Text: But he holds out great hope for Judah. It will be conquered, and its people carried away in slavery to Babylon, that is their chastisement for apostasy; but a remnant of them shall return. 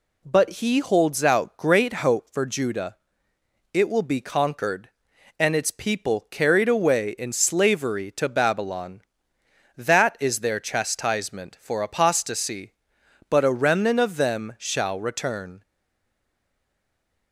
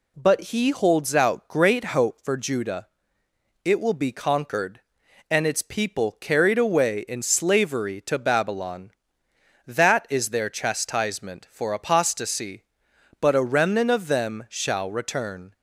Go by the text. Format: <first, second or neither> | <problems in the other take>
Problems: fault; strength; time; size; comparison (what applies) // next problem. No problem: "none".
second | stays silent after the last word; noticeable; from 15.6 s on; 1.7 s long